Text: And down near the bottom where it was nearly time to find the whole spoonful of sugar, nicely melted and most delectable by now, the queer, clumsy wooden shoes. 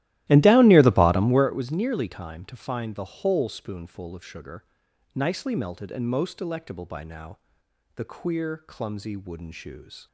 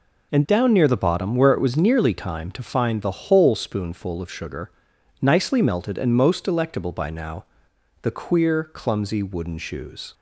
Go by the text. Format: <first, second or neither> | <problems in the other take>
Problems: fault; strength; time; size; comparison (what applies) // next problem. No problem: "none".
second | starts louder than the rest; strong; until 1.5 s; 15 dB